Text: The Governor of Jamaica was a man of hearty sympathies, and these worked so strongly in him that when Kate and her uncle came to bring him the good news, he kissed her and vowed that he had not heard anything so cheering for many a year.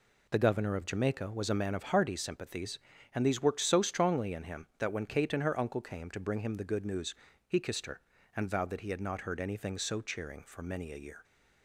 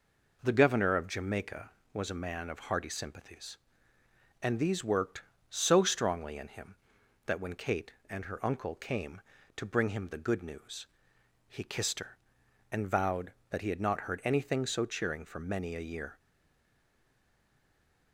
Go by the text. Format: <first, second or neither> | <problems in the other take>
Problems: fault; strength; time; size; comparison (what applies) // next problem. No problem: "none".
first | stays silent after the last word; noticeable; from 16.1 s on; 2.0 s long